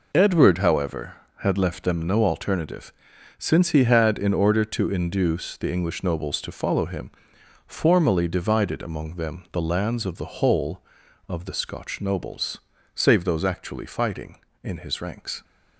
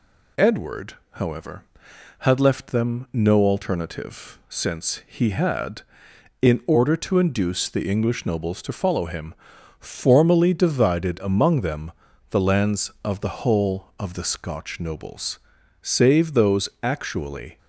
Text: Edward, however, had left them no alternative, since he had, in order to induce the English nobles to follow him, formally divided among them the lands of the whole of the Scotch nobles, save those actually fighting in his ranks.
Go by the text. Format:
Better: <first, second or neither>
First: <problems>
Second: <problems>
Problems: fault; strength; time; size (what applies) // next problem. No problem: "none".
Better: first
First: none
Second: pauses between "them" and "the"; at 11.9 s; 0.38 s long // stops before "fighting in his ranks"; at 17.5 s